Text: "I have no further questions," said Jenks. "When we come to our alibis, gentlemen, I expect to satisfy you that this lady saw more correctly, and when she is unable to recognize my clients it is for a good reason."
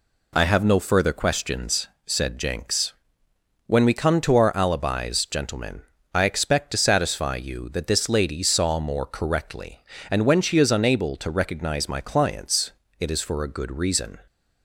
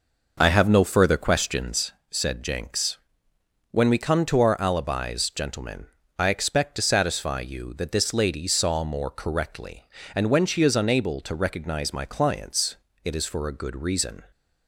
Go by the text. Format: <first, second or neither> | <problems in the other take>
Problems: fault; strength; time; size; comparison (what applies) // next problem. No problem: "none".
first | starts louder than the rest; noticeable; until 1.8 s; 5.5 dB // pauses between "clients" and "it"; slight; at 12.7 s; 0.28 s long; slight in the first